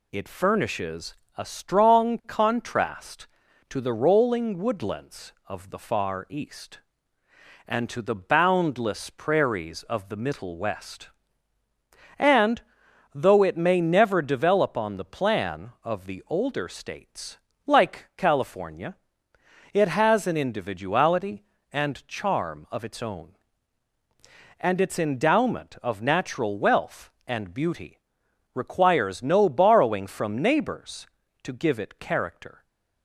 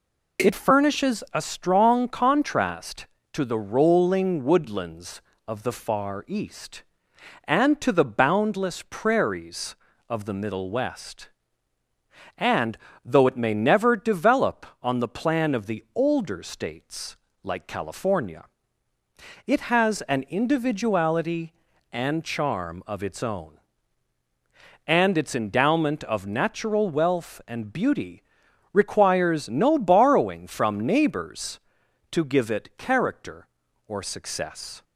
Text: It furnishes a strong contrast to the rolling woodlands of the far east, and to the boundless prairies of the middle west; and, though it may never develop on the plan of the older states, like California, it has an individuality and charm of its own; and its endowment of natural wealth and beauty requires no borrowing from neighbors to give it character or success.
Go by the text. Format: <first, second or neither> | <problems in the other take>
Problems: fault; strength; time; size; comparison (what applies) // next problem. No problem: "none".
second | pauses between "furnishes" and "a"; slight; at 1.1 s; 0.22 s long // pauses between "beauty" and "requires"; noticeable; at 27.9 s; 0.54 s long; noticeable in the second // stops before "or success"; at 32.6 s